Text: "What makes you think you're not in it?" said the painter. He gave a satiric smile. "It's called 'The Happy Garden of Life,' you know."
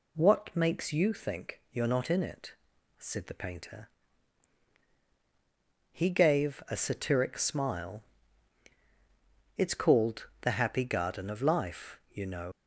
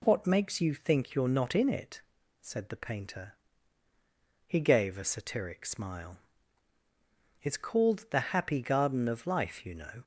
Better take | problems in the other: second | leaves "know" unfinished; at 12.5 s; 100 ms

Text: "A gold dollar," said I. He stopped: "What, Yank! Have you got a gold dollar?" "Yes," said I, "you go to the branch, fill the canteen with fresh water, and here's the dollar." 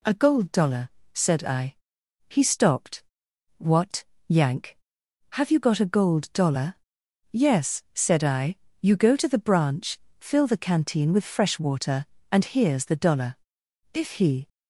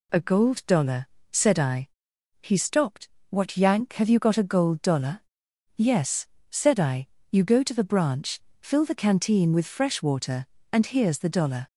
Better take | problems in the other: second | goes on to say "If he"; from 13.9 s on; 0.54 s long

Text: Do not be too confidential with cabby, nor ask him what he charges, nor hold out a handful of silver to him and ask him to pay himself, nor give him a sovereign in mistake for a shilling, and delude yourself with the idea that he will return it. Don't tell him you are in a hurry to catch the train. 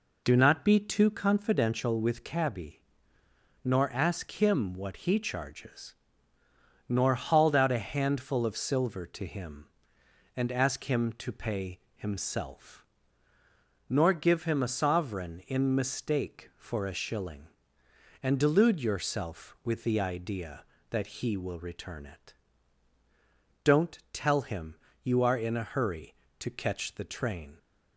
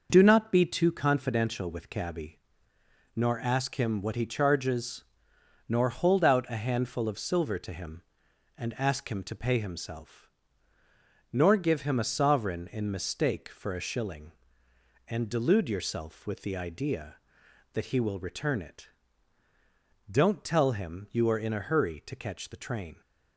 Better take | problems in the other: second | says "hauled" for "hold"; at 7.1 s // pauses between "pay" and "himself"; slight; at 11.7 s; 0.18 s long // pauses between "him" and "you"; slight; at 24.7 s; 0.26 s long

